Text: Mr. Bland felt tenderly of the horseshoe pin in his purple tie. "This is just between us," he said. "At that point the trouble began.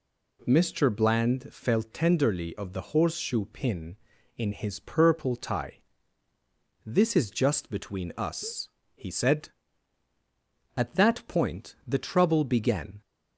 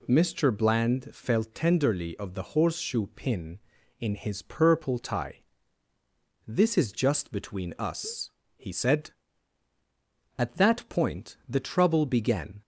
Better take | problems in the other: neither | none

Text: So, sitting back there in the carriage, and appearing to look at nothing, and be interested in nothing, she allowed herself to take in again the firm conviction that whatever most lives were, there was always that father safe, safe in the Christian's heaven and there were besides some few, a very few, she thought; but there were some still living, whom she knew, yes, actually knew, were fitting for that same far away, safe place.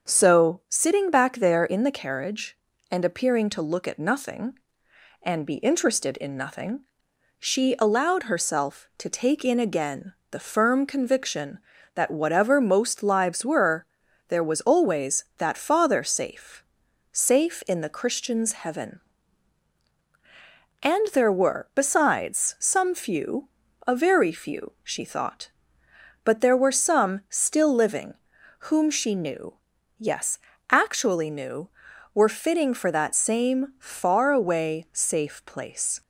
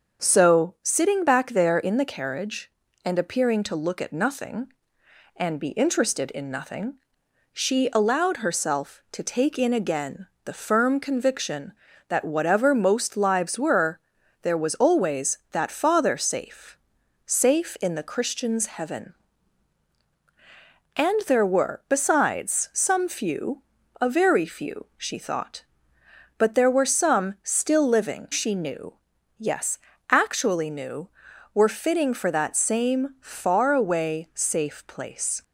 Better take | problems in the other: first | starts louder than the rest; until 1.3 s; 6.5 dB; also in the first // pauses between "again" and "the"; slight; at 10.2 s; 0.18 s long; slight in the first // skips "whom"; at 28.2 s

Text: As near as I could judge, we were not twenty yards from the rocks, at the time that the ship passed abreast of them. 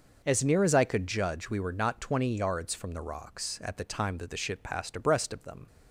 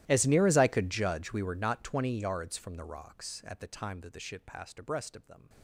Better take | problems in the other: first | gets quieter; strong; throughout; 25.5 dB

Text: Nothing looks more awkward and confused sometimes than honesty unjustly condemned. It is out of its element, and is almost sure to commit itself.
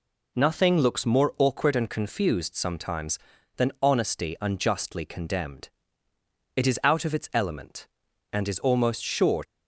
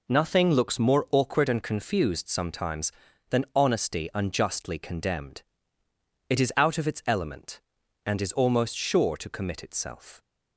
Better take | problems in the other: second | stops before "to commit itself"; at 9.4 s

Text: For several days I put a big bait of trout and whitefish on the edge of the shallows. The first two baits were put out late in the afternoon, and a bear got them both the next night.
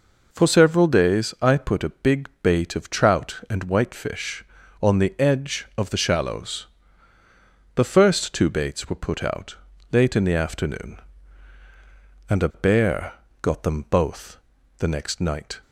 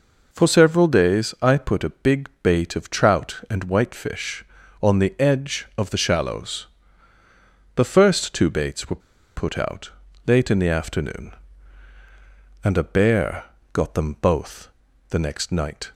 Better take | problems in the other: first | pauses between "were" and "put"; at 9.0 s; 0.36 s long // pauses between "out" and "late"; slight; at 9.9 s; 0.36 s long; slight in the first // pauses between "bear" and "got"; slight; at 13.4 s; 0.28 s long; slight in the first // pauses between "both" and "the"; at 14.6 s; 0.42 s long; also in the first

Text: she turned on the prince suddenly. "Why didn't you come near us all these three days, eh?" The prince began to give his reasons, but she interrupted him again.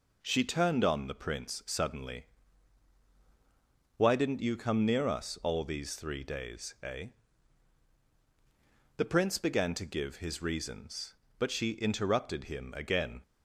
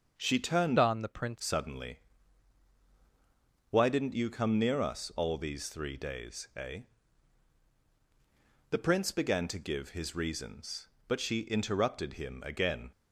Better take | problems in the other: first | starts louder than the rest; until 1.1 s; 6 dB // changes voice from "on" to "prince"; from 0.7 to 1.3 s; 0.6 s long

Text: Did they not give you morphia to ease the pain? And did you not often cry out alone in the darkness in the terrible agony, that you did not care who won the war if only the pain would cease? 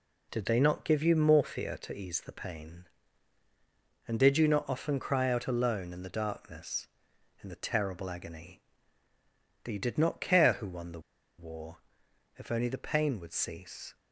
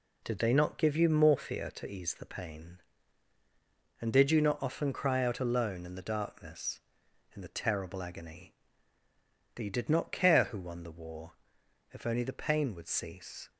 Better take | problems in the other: second | pauses between "the" and "war"; at 10.9 s; 0.39 s long // pauses between "war" and "if"; noticeable; at 11.7 s; 0.60 s long; noticeable in the second

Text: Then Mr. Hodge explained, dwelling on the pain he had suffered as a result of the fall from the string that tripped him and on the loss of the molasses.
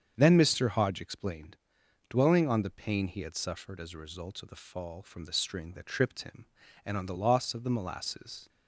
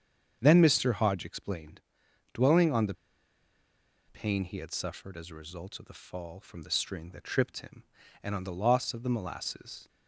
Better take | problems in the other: first | starts louder than the rest; strong; until 1.4 s; 7.5 dB; strong in the first // pauses between "the" and "pain"; at 2.9 s; 1.1 s long

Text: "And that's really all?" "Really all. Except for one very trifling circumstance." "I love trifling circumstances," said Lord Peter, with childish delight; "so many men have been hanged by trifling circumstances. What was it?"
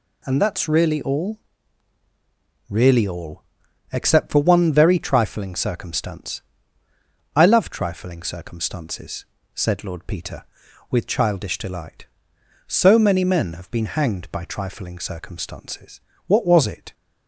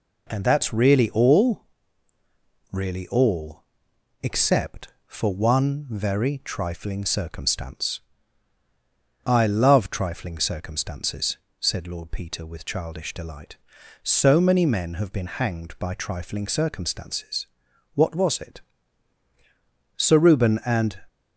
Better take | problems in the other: first | goes on to say "Sir Reuben and"; noticeable; from 19.9 s on; 1.0 s long

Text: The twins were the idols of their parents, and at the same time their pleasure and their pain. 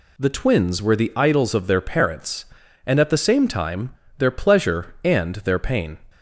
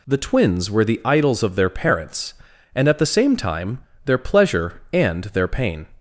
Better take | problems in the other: neither | pauses between "time" and "their"; slight; the same in both

